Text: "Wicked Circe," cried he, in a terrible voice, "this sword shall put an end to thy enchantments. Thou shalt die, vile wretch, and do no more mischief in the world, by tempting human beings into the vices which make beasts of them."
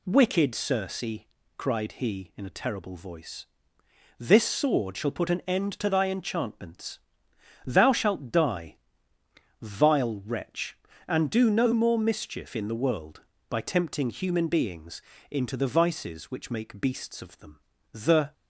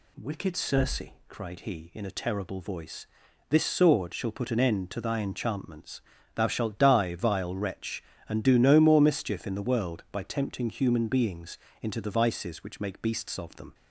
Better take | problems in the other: second | pauses between "beings" and "into"; slight; at 15.0 s; 0.30 s long; slight in the second // goes on to say "The"; slight; from 17.9 s on; 0.40 s long

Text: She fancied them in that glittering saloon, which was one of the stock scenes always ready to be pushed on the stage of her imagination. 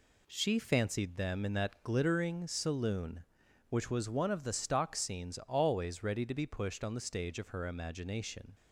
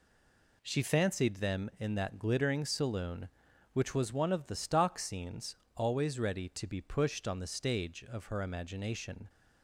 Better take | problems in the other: first | stays silent before the first word; slight; until 0.6 s; 0.6 s long // pauses between "scenes" and "always"; slight; at 5.5 s; 0.22 s long

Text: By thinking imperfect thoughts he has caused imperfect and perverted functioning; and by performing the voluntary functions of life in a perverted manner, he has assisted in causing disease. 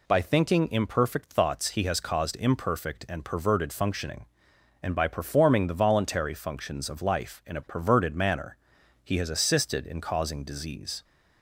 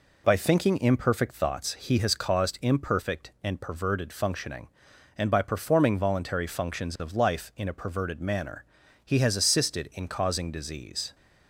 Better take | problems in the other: first | skips "the"; at 5.9 s

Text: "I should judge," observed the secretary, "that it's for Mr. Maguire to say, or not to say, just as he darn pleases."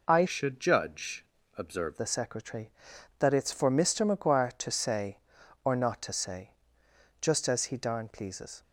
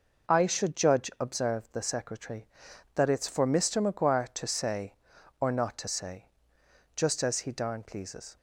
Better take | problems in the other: second | changes voice from "should" to "observed"; from 0.2 to 1.9 s; 1.7 s long

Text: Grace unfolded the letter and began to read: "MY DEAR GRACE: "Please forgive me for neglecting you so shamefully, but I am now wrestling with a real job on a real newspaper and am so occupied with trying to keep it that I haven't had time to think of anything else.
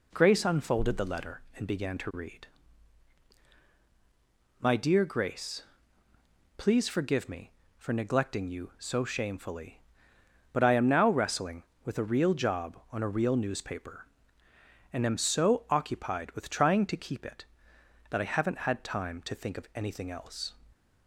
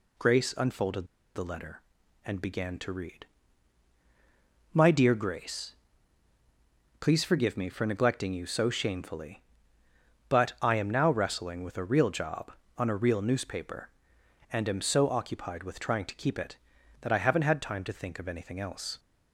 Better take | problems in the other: first | pauses between "unfolded" and "the"; slight; at 1.0 s; 0.30 s long

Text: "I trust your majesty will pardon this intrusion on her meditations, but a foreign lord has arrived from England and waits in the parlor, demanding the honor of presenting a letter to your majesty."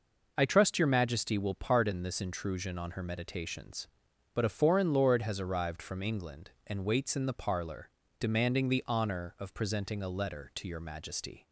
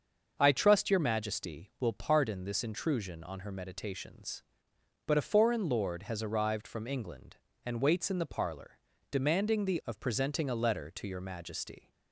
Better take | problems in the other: first | starts louder than the rest; until 1.4 s; 6.5 dB // skips "honor"; at 9.8 s

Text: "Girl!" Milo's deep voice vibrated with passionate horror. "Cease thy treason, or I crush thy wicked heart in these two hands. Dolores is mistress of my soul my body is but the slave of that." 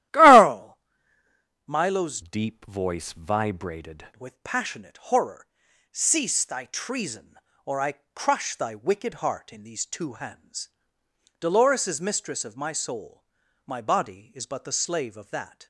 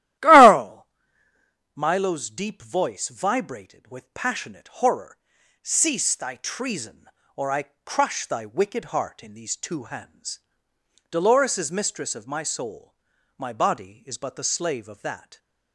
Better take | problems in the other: second | starts louder than the rest; strong; until 1.9 s; 14 dB; strong in the second // changes voice from "deep" to "vibrated"; from 2.2 to 4.0 s; 1.8 s long // pauses between "I" and "crush"; slight; at 7.9 s; 0.20 s long; slight in the second // pauses between "soul" and "my"; at 13.2 s; 0.42 s long; also in the second

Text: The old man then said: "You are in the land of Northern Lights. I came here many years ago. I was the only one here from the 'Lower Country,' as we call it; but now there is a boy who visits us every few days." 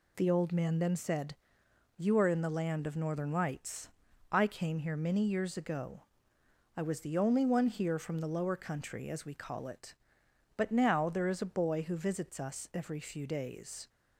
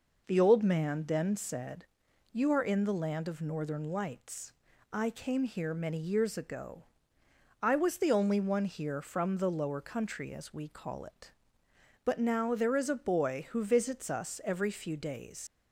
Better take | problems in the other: first | leaves "days" unfinished; at 15.4 s; 90 ms

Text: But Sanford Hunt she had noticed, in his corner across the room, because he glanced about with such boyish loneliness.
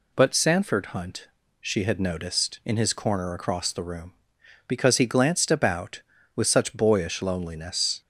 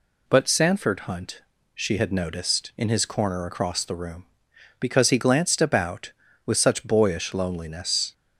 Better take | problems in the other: neither | pauses between "Hunt" and "she"; slight; the same in both

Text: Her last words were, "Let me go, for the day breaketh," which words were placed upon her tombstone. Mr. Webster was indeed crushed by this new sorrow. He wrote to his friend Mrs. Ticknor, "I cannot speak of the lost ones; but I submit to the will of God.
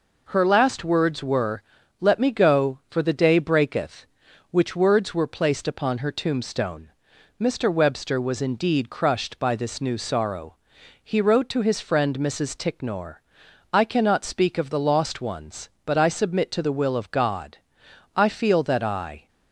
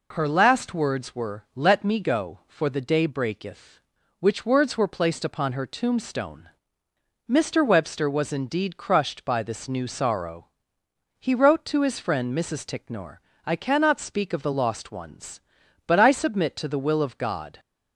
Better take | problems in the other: second | goes on to say "I feel that I"; noticeable; from 18.1 s on; 1.1 s long

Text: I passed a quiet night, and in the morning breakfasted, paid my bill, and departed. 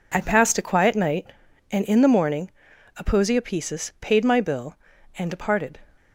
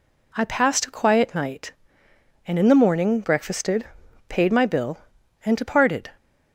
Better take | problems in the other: second | says "aposiopesis" for "breakfasted"; at 2.9 s

